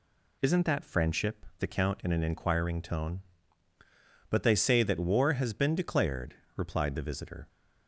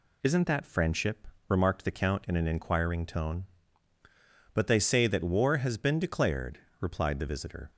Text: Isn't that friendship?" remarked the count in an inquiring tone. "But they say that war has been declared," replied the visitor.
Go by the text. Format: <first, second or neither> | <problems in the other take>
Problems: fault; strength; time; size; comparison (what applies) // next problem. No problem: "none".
second | skips "remarked"; at 1.5 s